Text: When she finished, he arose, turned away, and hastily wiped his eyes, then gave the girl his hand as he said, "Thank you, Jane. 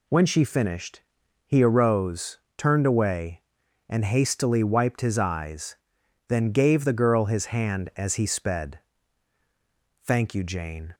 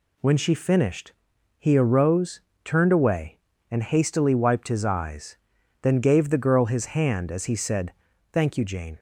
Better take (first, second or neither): second